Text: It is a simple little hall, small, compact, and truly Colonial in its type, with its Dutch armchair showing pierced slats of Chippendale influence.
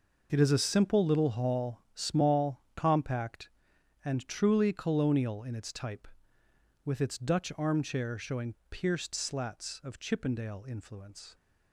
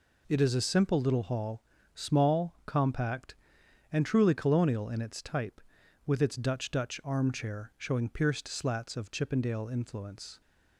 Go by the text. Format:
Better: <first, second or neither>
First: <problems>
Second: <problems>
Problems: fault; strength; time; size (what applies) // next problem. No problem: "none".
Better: first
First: none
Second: says "Dutch" twice; at 6.7 s